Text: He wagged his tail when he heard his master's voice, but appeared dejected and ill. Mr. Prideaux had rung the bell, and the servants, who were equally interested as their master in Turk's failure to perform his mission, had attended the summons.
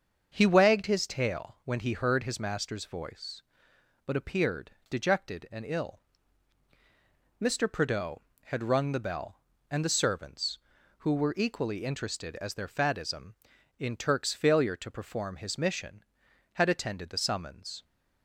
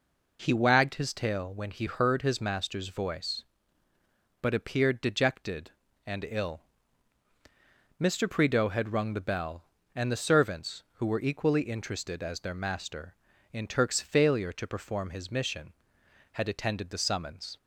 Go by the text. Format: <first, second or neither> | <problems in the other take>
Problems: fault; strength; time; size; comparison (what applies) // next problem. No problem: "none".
second | starts louder than the rest; until 1.3 s; 6.5 dB // pauses between "appeared" and "dejected"; slight; at 4.7 s; 0.18 s long // says "faddism" for "master"; at 12.6 s